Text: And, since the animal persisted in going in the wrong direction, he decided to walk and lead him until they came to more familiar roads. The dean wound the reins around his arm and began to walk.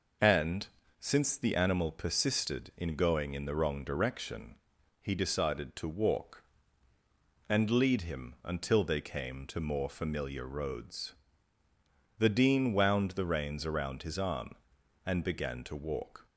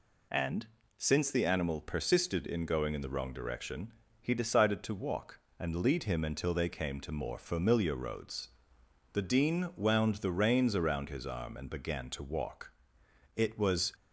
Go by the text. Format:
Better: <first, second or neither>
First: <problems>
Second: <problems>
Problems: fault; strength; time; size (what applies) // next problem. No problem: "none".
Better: first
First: none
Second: goes on to say "It was"; from 13.3 s on; 0.58 s long